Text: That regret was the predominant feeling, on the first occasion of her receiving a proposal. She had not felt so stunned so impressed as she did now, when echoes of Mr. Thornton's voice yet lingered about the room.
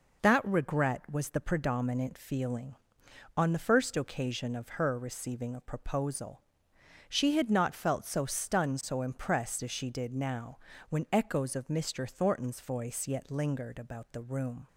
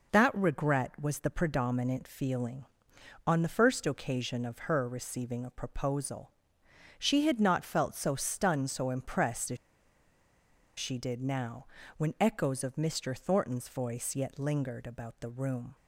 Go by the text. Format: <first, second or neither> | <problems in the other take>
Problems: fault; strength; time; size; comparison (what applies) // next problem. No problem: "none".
first | pauses between "as" and "she"; at 9.5 s; 1.2 s long